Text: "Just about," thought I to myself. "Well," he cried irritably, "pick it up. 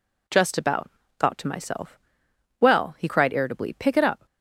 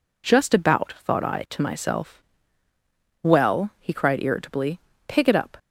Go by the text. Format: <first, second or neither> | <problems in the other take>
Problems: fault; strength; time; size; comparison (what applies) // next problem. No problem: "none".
second | skips "I"; at 1.3 s